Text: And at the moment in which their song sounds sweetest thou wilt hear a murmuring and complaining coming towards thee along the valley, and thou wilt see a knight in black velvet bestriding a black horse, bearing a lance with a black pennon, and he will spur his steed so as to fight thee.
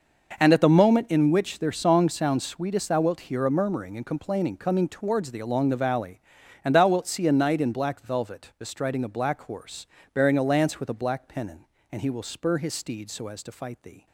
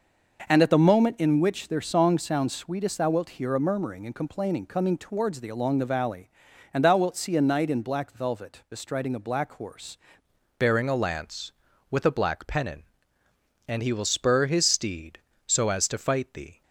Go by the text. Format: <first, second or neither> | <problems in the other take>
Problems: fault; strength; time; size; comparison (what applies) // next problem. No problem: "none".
first | changes voice at "bearing"; from 10.5 s on; 6.1 s long